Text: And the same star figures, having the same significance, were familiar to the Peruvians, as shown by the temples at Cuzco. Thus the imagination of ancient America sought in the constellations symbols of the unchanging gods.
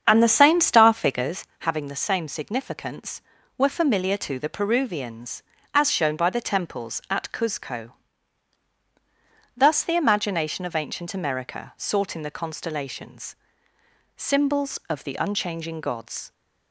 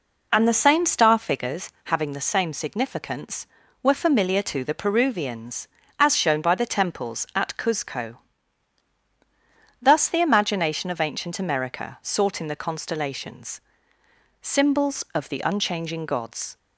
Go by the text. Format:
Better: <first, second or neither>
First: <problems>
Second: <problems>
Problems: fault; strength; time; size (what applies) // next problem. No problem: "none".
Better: second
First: starts louder than the rest; strong; until 1.4 s; 7.5 dB // pauses between "constellations" and "symbols"; noticeable; at 13.3 s; 0.84 s long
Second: pauses between "constellations" and "symbols"; noticeable; at 13.5 s; 0.84 s long